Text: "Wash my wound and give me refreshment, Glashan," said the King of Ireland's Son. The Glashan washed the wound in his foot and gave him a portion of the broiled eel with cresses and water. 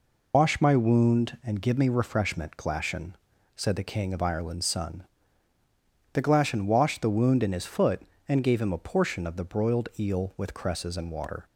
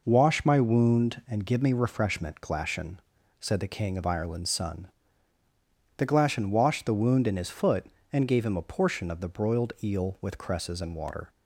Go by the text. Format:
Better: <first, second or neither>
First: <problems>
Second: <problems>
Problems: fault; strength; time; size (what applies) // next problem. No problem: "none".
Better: second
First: loses the start of "Wash"; at 0.3 s; 135 ms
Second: none